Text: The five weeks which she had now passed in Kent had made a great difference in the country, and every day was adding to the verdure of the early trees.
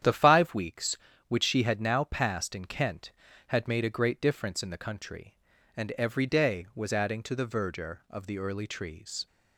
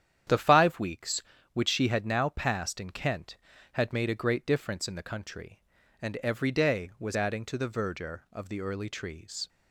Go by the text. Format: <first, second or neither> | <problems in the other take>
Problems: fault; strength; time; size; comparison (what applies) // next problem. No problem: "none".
neither | starts louder than the rest; strong; the same in both